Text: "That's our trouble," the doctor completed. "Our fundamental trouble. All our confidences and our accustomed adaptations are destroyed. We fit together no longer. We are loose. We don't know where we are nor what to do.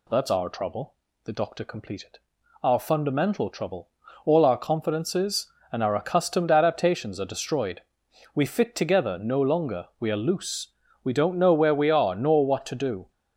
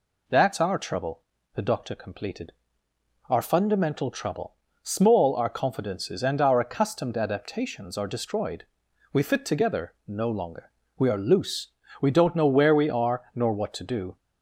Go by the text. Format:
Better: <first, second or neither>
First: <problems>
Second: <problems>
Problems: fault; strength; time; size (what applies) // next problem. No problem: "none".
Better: first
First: none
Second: says "Small" for "All"; at 4.8 s